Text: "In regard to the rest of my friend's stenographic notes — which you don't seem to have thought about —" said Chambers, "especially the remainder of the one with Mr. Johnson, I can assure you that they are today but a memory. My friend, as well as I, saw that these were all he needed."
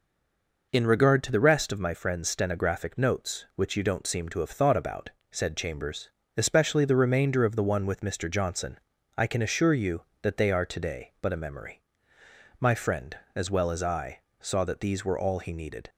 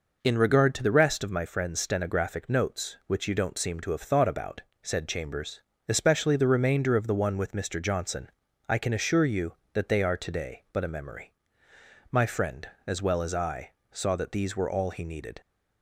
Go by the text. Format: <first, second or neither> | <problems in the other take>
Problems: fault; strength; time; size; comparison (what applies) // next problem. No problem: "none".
second | stays silent before the first word; slight; until 0.7 s; 0.7 s long